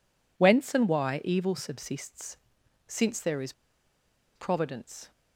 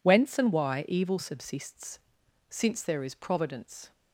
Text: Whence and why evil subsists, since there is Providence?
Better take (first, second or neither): second